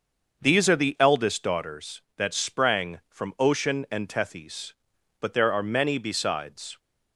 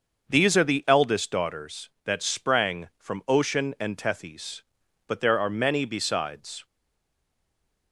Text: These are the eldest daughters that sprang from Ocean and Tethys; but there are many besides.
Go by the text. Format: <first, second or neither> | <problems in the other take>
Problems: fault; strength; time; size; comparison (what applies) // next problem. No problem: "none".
first | starts louder than the rest; until 1.3 s; 6 dB; also in the first // stays silent after the last word; noticeable; from 6.6 s on; 1.3 s long